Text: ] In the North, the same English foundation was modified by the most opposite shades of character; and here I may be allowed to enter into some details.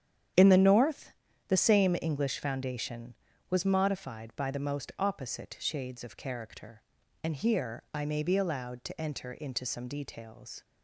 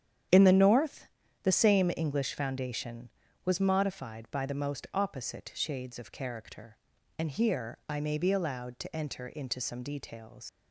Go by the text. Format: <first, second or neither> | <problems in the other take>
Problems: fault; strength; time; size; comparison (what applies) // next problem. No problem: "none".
first | starts louder than the rest; strong; until 1.6 s; 9 dB; strong in the first // leaves "details" unfinished; at 10.4 s; 100 ms